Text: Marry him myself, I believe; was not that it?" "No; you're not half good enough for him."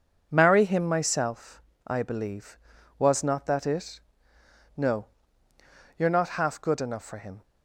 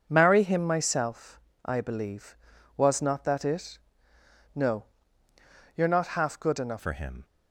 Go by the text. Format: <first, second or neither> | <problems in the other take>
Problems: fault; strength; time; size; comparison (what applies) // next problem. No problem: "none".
first | changes voice at "for"; from 6.7 s on; 0.5 s long